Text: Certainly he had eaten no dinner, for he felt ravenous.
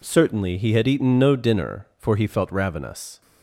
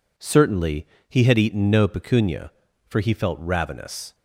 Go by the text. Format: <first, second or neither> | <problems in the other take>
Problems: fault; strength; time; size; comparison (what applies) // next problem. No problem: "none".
first | pauses between "Certainly" and "he"; slight; at 0.8 s; 0.22 s long // says "pecunia" for "dinner"; at 1.8 s